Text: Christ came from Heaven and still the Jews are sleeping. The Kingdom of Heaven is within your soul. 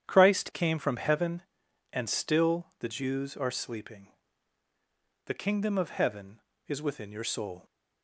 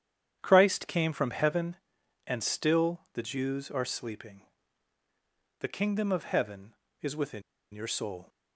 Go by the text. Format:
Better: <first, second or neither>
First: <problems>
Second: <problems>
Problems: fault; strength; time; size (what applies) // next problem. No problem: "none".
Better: first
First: starts louder than the rest; strong; until 1.0 s; 9 dB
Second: starts louder than the rest; strong; until 1.4 s; 9 dB // pauses between "within" and "your"; slight; at 7.4 s; 0.32 s long